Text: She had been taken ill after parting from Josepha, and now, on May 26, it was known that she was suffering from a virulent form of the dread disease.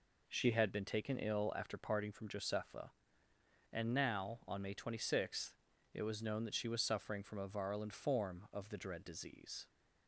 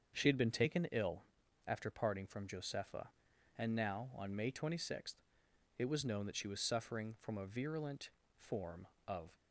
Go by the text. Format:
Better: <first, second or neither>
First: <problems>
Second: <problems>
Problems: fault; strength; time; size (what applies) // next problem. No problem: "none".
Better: first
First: none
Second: starts louder than the rest; until 1.2 s; 6.5 dB // pauses between "ill" and "after"; at 1.2 s; 0.42 s long // pauses between "virulent" and "form"; slight; at 8.1 s; 0.28 s long // stops before "the dread disease"; at 9.3 s